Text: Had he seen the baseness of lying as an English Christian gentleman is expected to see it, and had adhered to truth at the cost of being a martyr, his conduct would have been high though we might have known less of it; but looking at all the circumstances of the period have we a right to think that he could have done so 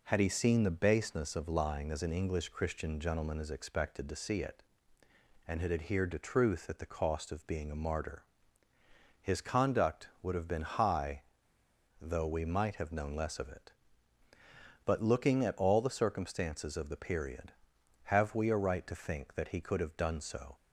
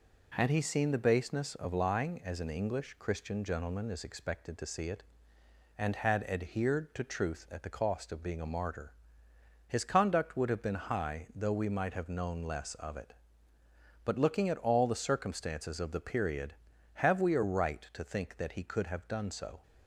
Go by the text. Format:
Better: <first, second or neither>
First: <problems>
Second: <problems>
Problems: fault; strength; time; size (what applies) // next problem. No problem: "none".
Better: second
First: pauses between "high" and "though"; noticeable; at 11.2 s; 0.79 s long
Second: none